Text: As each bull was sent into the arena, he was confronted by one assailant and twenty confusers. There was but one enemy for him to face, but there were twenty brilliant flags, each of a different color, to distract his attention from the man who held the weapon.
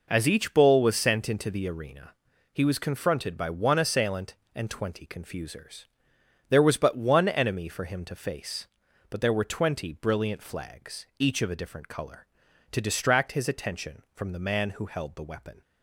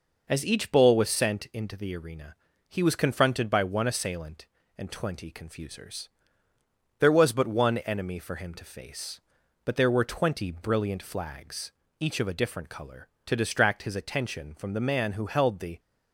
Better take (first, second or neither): first